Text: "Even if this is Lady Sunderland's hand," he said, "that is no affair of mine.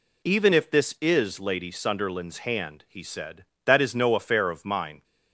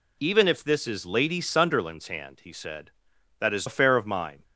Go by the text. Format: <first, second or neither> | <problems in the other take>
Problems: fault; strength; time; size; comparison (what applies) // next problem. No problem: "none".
first | skips "no"; at 3.6 s